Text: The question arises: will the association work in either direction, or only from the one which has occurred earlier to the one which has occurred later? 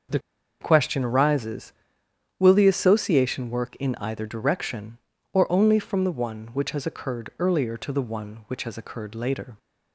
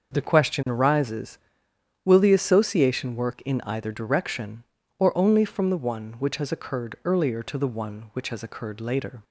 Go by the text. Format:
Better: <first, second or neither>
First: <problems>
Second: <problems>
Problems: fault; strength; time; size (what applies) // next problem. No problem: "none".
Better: second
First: starts louder than the rest; until 1.5 s; 6 dB // pauses between "The" and "question"; at 0.1 s; 0.42 s long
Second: starts louder than the rest; until 1.1 s; 6 dB